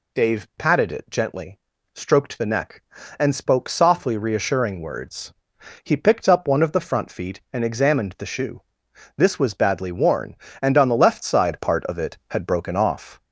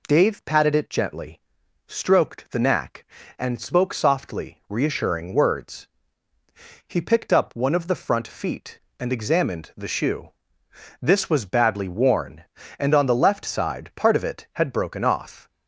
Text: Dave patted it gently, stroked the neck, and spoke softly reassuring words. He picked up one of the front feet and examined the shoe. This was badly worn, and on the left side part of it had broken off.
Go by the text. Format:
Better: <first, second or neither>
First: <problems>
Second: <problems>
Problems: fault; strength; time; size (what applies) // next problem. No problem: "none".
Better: first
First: none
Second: says "knack" for "neck"; at 2.5 s